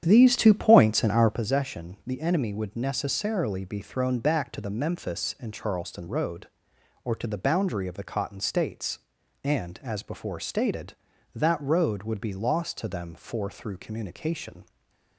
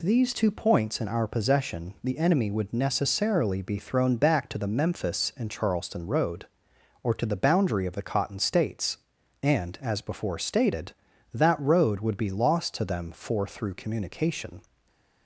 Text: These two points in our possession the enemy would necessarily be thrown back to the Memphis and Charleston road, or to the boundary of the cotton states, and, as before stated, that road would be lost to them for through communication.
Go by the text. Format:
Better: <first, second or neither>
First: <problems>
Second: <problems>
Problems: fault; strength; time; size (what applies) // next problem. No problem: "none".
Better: second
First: starts louder than the rest; strong; until 1.4 s; 9 dB // stays silent after the last word; slight; from 14.6 s on; 0.5 s long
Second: stays silent after the last word; slight; from 14.6 s on; 0.6 s long